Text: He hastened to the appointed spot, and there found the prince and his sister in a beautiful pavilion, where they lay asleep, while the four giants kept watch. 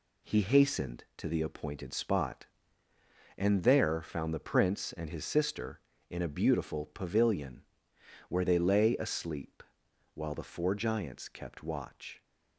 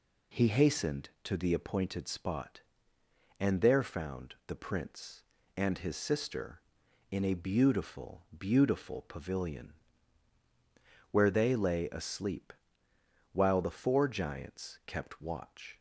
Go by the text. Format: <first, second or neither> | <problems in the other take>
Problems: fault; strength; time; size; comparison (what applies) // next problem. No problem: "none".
first | says "beautiful" twice; at 8.3 s